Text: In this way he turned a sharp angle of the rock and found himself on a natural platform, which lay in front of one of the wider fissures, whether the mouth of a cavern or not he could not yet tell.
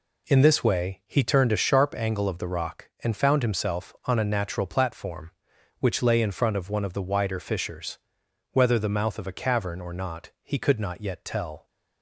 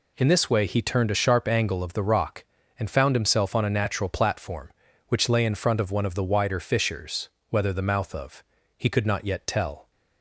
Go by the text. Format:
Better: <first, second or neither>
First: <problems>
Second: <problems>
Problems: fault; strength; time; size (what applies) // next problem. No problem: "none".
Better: first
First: none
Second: skips "a cavern or not"; at 8.5 s